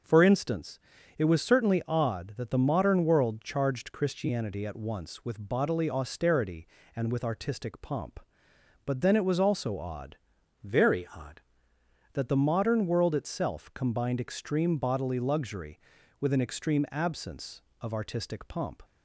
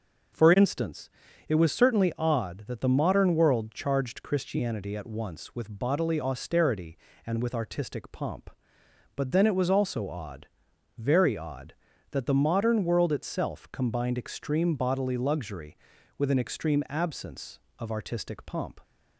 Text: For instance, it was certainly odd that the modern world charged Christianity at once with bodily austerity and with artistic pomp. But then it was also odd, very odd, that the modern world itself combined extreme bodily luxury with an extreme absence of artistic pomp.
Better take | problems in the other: second | starts louder than the rest; noticeable; until 1.4 s; 6 dB // changes voice from "very" to "odd"; from 10.6 to 11.3 s; 0.7 s long

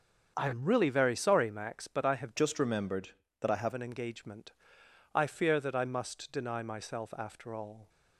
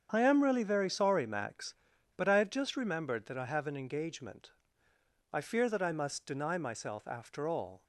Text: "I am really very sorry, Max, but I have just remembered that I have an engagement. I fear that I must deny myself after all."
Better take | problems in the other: second | starts louder than the rest; until 1.3 s; 7 dB; strong in the second // changes voice from "just" to "have"; from 2.3 to 3.7 s; 1.4 s long

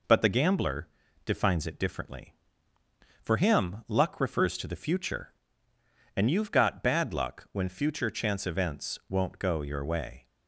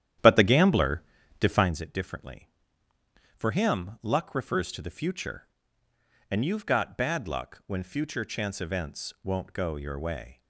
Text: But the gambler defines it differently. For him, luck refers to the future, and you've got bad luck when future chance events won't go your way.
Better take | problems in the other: first | starts louder than the rest; strong; until 1.7 s; 10.5 dB // pauses between "gambler" and "defines"; slight; at 1.0 s; 0.36 s long; slight in the first

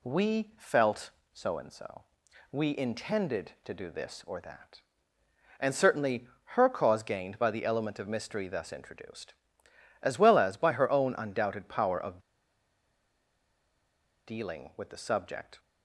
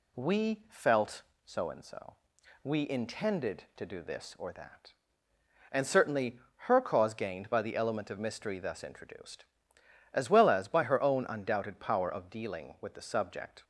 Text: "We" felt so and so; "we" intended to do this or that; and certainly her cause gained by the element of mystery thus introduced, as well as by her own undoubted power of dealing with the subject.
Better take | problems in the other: second | pauses between "certainly" and "her"; slight; at 6.2 s; 0.30 s long; slight in the second // pauses between "of" and "dealing"; strong; at 12.1 s; 2.0 s long

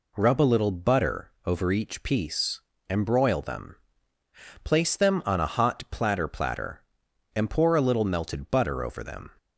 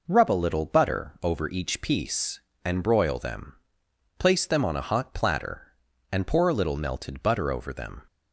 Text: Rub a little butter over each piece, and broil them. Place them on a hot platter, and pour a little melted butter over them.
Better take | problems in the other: second | says "platter" twice; at 6.2 s

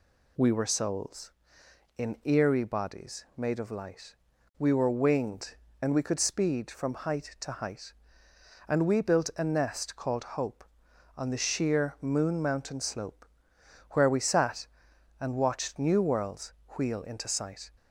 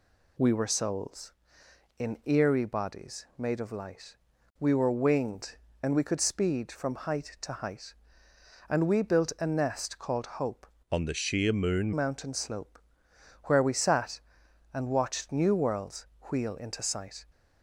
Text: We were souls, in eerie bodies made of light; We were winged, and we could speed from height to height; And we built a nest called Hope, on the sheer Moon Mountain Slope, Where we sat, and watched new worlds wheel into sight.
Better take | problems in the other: first | changes voice from "on" to "Moon"; from 10.9 to 11.9 s; 1.0 s long // pauses between "worlds" and "wheel"; slight; at 16.0 s; 0.18 s long; slight in the first

